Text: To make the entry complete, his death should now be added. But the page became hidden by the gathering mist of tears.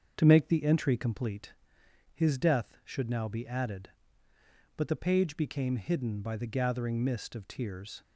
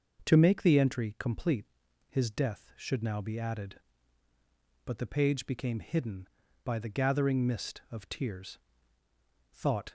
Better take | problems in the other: first | starts louder than the rest; noticeable; until 1.3 s; 6 dB; also in the first // goes on to say "Thought"; slight; from 9.5 s on; 0.40 s long

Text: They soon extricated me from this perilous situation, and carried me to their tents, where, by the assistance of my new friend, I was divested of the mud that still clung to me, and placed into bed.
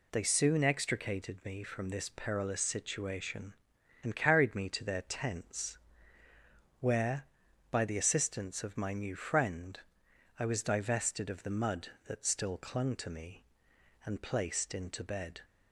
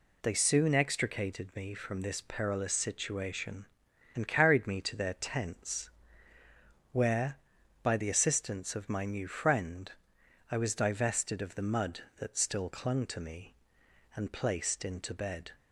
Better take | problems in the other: neither | none

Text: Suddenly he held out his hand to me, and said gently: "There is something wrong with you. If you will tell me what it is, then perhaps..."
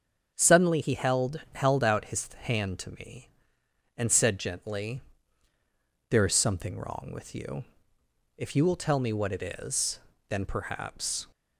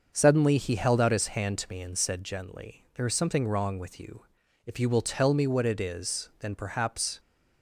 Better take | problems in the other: second | starts louder than the rest; strong; until 1.3 s; 8 dB; also in the second // says "held" twice; at 1.5 s

